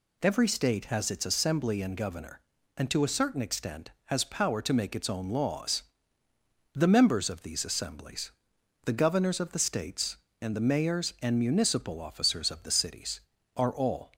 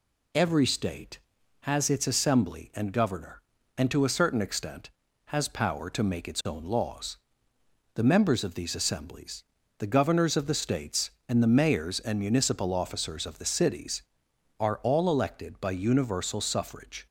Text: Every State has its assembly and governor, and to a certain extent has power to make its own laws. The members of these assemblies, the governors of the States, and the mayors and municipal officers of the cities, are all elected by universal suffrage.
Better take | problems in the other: second | stops before "elected by universal suffrage"; at 14.1 s

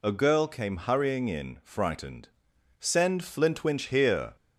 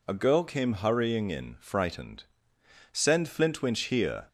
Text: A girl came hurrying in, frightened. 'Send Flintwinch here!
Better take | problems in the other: neither | none

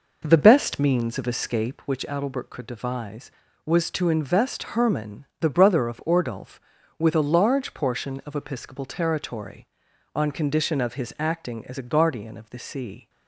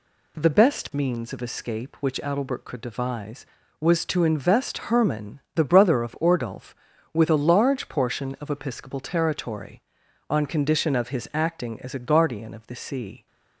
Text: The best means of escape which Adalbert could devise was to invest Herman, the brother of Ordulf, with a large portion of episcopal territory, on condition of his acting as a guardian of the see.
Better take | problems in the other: second | starts louder than the rest; noticeable; until 1.8 s; 5 dB

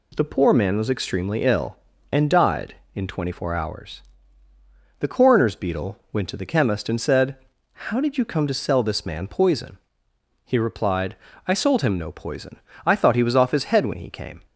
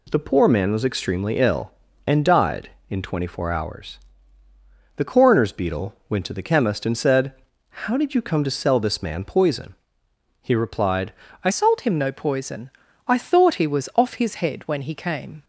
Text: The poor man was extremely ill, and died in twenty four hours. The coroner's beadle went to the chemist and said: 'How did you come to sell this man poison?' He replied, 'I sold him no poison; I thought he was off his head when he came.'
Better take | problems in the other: first | changes voice at "sold"; from 11.5 s on; 3.9 s long

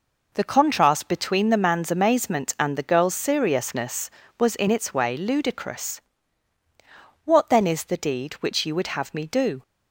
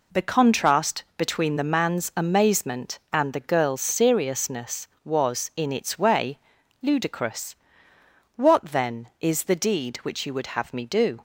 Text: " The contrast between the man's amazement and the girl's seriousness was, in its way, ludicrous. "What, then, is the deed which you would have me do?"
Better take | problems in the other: neither | none

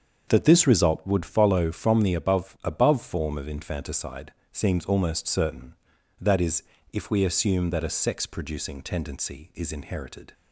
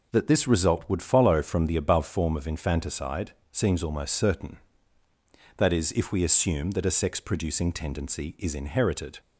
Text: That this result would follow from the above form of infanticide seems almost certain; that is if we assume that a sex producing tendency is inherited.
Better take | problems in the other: second | starts louder than the rest; until 1.3 s; 7 dB // says "above" twice; at 2.6 s // pauses between "infanticide" and "seems"; slight; at 4.3 s; 0.22 s long; slight in the second // pauses between "is" and "if"; slight; at 6.6 s; 0.32 s long

